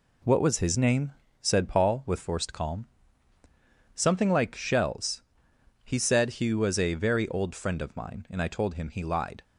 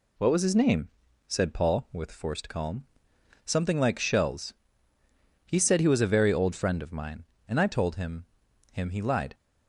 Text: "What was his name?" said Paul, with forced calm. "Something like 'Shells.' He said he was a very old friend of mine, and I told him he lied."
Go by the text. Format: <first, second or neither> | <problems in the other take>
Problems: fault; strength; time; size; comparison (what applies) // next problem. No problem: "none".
first | says "him" twice; at 8.7 s